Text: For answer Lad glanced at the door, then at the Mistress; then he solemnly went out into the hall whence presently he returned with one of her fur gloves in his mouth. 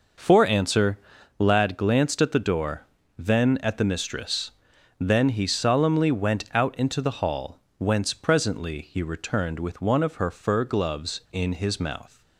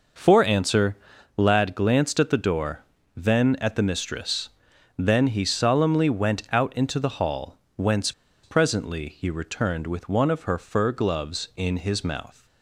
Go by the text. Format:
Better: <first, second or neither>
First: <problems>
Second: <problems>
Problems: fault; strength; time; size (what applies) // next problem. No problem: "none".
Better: first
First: pauses between "answer" and "Lad"; at 0.9 s; 0.40 s long // pauses between "hall" and "whence"; slight; at 7.6 s; 0.16 s long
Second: pauses between "answer" and "Lad"; at 0.9 s; 0.40 s long // pauses between "hall" and "whence"; slight; at 7.5 s; 0.16 s long // pauses between "whence" and "presently"; slight; at 8.1 s; 0.32 s long